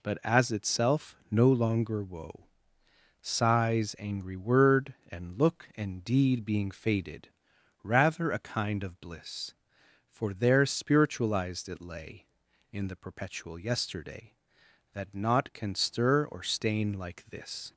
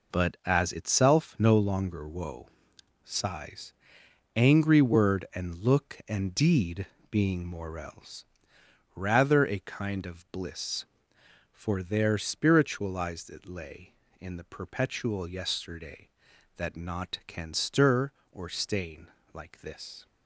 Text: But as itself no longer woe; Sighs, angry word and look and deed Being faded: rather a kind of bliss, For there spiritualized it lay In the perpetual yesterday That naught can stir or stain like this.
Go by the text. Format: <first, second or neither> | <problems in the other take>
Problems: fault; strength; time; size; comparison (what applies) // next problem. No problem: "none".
first | pauses between "deed" and "Being"; slight; at 6.8 s; 0.24 s long // says "morels" for "faded"; at 7.4 s // pauses between "stain" and "like"; slight; at 19.0 s; 0.24 s long